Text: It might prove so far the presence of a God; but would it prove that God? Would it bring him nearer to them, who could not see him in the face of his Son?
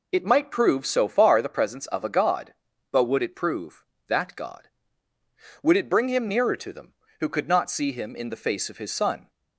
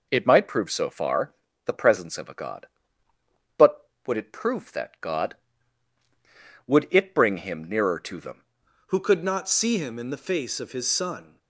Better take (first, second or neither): first